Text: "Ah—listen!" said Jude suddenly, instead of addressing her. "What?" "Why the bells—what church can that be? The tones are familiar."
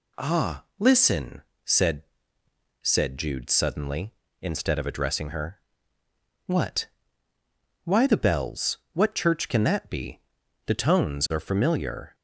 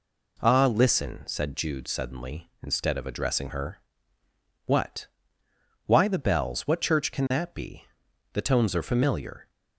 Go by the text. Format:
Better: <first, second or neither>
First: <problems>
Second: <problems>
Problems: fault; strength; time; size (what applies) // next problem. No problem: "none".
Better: second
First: says "said" twice; at 2.8 s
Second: none